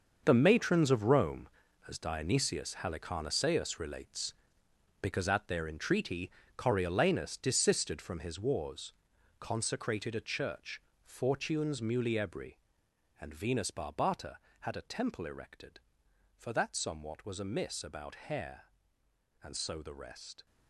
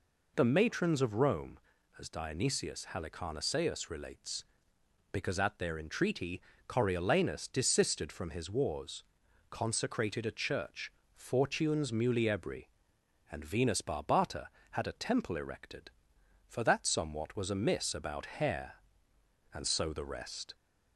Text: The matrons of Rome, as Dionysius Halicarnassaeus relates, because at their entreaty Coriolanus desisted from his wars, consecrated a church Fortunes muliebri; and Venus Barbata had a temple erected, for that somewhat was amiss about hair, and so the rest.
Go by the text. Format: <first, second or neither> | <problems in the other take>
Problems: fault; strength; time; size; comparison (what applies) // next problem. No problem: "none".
second | gets quieter; strong; throughout; 12 dB // pauses between "entreaty" and "Coriolanus"; slight; at 6.3 s; 0.24 s long; slight in the second // pauses between "church" and "Fortunes"; slight; at 10.7 s; 0.24 s long; slight in the second